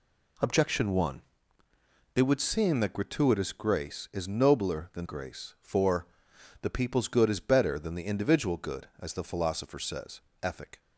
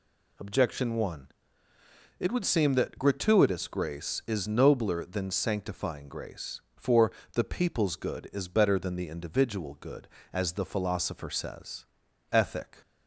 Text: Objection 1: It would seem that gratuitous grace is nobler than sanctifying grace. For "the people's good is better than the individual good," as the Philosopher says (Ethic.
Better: second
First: skips "sanctifying"; at 5.0 s // pauses between "For" and "the"; noticeable; at 6.0 s; 0.54 s long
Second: pauses between "For" and "the"; slight; at 7.1 s; 0.22 s long

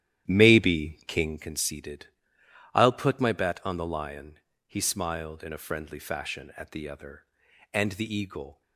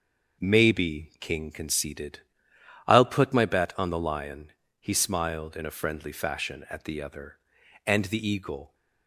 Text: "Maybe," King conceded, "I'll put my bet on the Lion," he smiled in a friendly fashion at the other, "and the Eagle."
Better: second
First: starts louder than the rest; strong; until 1.6 s; 11.5 dB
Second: none

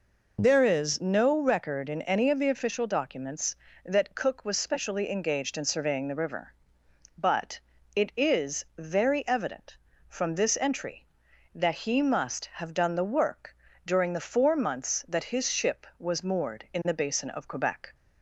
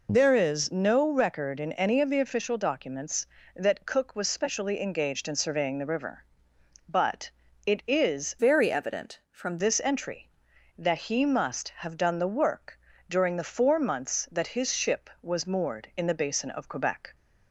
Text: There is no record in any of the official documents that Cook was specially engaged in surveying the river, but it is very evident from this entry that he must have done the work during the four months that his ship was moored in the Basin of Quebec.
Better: first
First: pauses between "but" and "it"; slight; at 7.5 s; 0.34 s long // pauses between "work" and "during"; slight; at 13.5 s; 0.32 s long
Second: pauses between "but" and "it"; slight; at 7.3 s; 0.34 s long // changes voice from "very" to "from"; from 8.3 to 9.5 s; 1.2 s long // pauses between "work" and "during"; slight; at 12.7 s; 0.32 s long

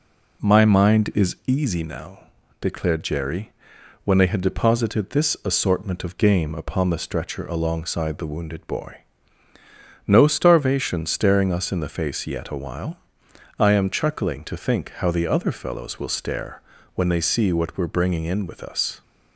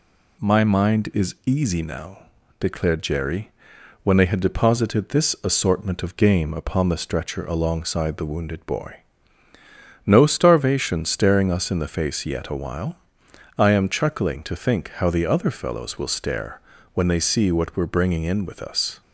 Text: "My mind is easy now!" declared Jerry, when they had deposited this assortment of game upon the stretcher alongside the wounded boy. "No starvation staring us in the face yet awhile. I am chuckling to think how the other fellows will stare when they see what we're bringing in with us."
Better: second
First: starts louder than the rest; slight; until 1.6 s; 3 dB // pauses between "stare" and "when"; slight; at 16.6 s; 0.34 s long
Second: pauses between "stare" and "when"; slight; at 16.6 s; 0.34 s long

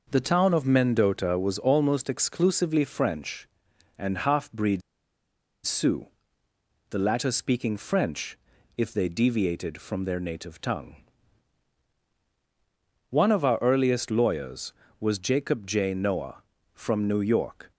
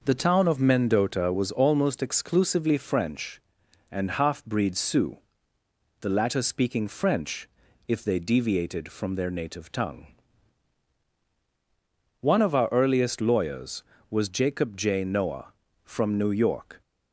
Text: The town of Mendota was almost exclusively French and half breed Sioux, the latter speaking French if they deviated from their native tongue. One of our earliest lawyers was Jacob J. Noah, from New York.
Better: second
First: pauses between "breed" and "Sioux"; noticeable; at 4.8 s; 0.83 s long // pauses between "French" and "if"; at 8.3 s; 0.40 s long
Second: pauses between "French" and "if"; at 7.4 s; 0.40 s long

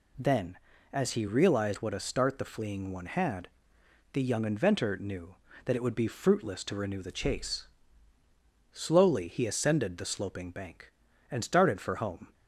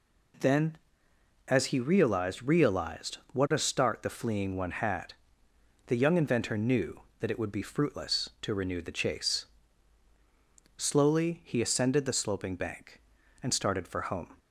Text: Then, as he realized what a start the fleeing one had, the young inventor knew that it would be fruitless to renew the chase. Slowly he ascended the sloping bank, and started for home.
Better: first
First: none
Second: says "realized" twice; at 2.4 s

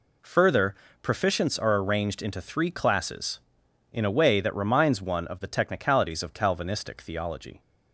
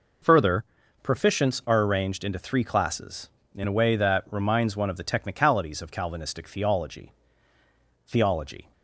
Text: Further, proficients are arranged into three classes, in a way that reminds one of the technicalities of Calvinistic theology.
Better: first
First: none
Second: says "theology" twice; at 8.0 s

